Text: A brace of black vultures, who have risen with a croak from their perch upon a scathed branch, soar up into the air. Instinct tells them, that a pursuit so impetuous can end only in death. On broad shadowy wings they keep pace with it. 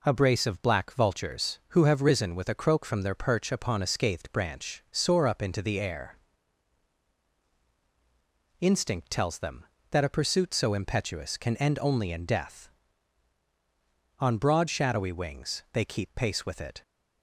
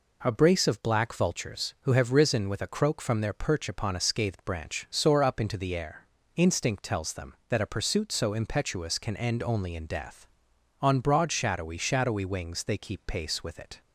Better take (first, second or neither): first